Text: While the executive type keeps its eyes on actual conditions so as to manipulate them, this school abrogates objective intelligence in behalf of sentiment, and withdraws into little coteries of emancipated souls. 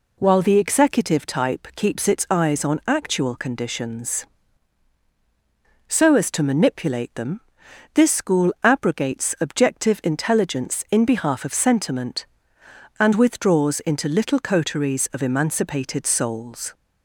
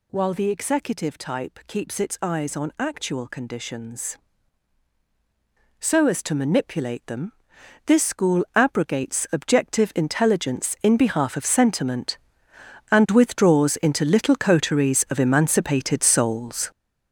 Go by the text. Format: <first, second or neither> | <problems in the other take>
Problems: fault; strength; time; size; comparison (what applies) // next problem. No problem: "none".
first | gets louder; strong; throughout; 9.5 dB